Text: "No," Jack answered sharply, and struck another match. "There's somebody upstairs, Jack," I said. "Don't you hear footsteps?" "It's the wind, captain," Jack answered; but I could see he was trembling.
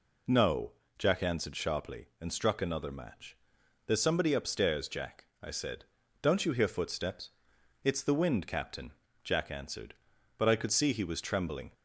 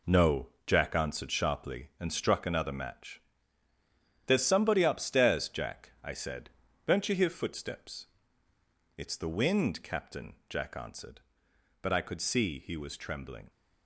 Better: first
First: none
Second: gets quieter; strong; throughout; 8.5 dB

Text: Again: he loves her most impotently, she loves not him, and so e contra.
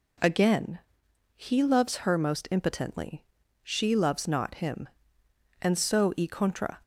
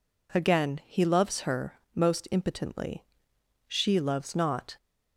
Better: first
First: none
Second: stops before "him and so e contra"; at 4.7 s

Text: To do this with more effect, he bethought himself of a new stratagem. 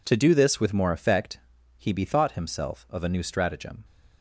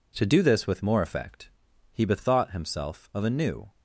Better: first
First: none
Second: stops before "stratagem"; at 3.6 s

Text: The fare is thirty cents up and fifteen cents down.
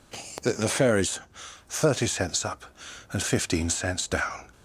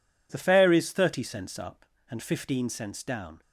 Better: second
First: says "The" twice; at 0.5 s // pauses between "is" and "thirty"; noticeable; at 1.1 s; 0.50 s long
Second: none

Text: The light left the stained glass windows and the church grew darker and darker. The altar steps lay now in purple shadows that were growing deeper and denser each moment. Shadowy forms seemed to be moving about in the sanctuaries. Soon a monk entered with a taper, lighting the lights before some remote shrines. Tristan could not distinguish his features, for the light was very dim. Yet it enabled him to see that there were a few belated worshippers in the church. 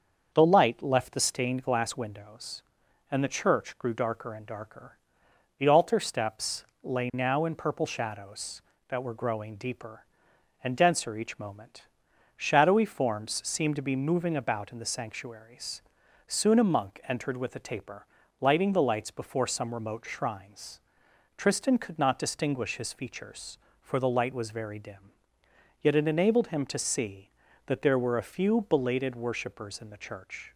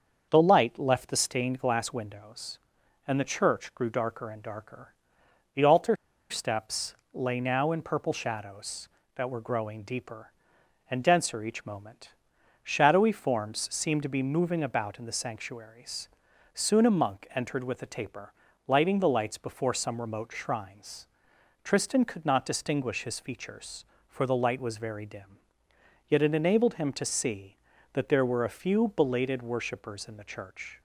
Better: first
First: starts louder than the rest; until 1.3 s; 6.5 dB // pauses between "steps" and "lay"; slight; at 6.6 s; 0.20 s long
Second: starts louder than the rest; until 1.3 s; 6.5 dB // pauses between "altar" and "steps"; slight; at 5.9 s; 0.35 s long // pauses between "steps" and "lay"; slight; at 6.9 s; 0.20 s long

